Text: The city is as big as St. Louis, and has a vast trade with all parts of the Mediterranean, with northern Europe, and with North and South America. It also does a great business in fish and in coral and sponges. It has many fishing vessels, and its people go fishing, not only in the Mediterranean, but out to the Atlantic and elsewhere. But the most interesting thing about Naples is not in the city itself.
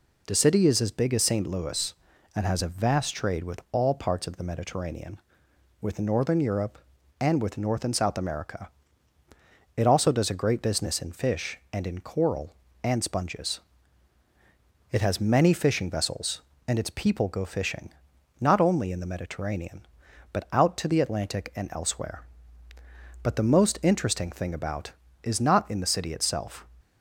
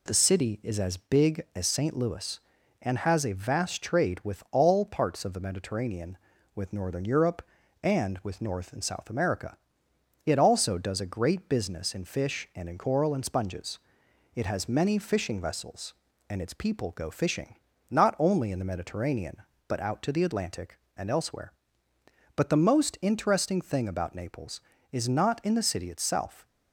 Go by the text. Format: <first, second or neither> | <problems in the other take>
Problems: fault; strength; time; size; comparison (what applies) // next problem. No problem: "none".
second | skips "Naples"; at 25.0 s